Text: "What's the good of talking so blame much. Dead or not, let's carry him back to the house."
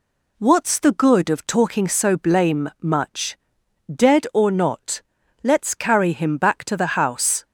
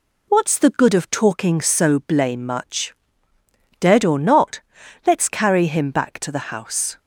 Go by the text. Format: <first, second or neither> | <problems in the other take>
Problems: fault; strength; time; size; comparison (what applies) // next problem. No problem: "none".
neither | none